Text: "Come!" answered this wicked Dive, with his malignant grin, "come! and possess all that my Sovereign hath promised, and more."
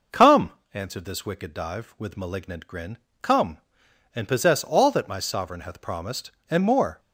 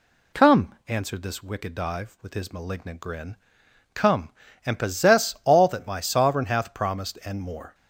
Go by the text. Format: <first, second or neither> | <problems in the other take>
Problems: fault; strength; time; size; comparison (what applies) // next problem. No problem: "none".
second | skips "his"; at 2.1 s